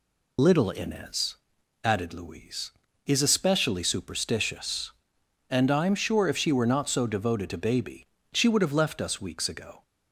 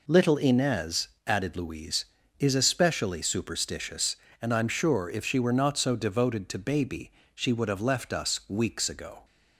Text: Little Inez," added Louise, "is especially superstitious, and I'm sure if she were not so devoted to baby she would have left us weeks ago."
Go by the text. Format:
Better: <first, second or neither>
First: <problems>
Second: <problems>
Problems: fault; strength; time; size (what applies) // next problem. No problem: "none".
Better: second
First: loses the start of "Little"; at 0.3 s; 35 ms // pauses between "baby" and "she"; slight; at 8.0 s; 0.26 s long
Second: pauses between "baby" and "she"; slight; at 7.1 s; 0.24 s long